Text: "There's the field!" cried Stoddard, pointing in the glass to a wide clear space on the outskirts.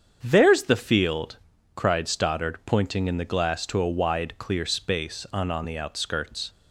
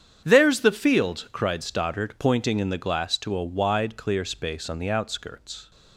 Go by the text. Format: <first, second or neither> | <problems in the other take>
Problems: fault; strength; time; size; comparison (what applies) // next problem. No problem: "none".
second | starts louder than the rest; strong; until 1.2 s; 7.5 dB; strong in the second // says "on" twice; at 5.4 s